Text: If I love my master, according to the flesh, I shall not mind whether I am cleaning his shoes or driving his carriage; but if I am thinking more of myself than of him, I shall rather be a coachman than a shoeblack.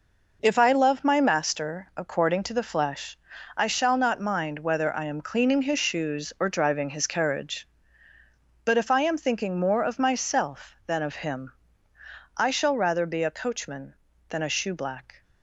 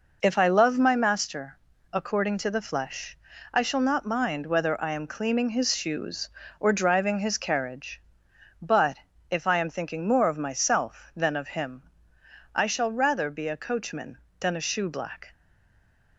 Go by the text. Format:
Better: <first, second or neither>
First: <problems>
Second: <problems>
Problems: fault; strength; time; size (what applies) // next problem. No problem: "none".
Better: first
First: none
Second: pauses between "but" and "if"; slight; at 8.9 s; 0.32 s long // stays silent after the last word; slight; from 15.3 s on; 0.8 s long